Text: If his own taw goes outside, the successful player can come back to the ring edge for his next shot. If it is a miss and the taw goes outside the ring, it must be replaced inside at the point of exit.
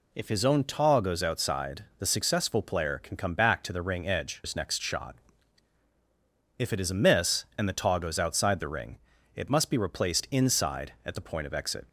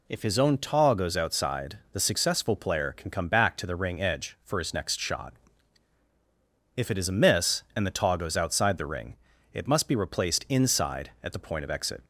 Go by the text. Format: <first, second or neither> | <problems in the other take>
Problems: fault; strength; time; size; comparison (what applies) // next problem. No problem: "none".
second | skips "for"; at 4.4 s